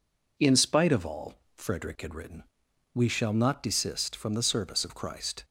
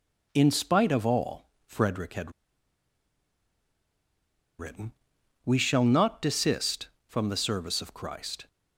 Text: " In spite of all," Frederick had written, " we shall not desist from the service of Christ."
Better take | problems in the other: first | pauses between "had" and "written"; strong; at 2.3 s; 2.2 s long

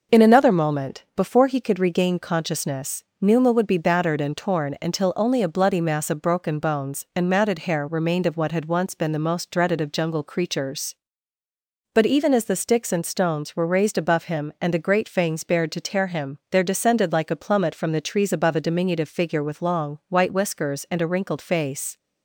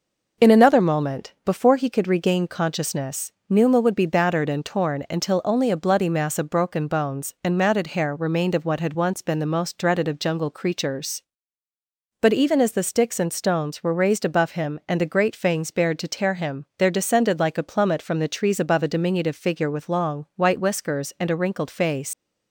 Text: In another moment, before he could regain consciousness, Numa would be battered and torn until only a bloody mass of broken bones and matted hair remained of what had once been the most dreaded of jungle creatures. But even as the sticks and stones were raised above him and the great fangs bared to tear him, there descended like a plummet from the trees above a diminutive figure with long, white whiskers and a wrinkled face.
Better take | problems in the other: first | leaves "face" unfinished; at 22.1 s; 130 ms

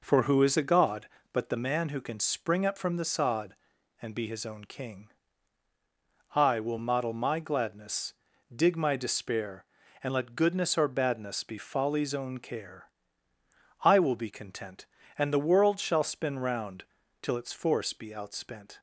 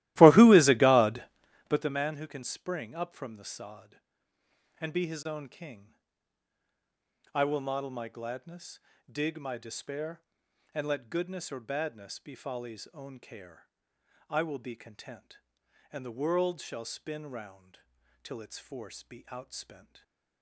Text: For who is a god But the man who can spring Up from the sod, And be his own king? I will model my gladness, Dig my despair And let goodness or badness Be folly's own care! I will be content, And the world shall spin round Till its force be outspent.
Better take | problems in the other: first | starts louder than the rest; strong; until 1.9 s; 16.5 dB // pauses between "round" and "Till"; noticeable; at 17.7 s; 0.46 s long; also in the first // stays silent after the last word; slight; from 19.7 s on; 0.7 s long

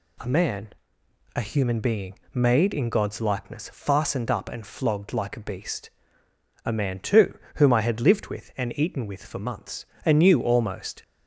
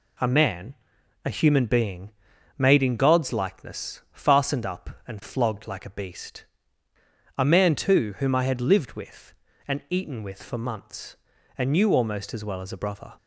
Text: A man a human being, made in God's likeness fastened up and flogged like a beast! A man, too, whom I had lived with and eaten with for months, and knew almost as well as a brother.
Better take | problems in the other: second | pauses between "man" and "a"; noticeable; at 0.7 s; 0.66 s long; noticeable in the second // stops before "as well as a brother"; at 11.0 s

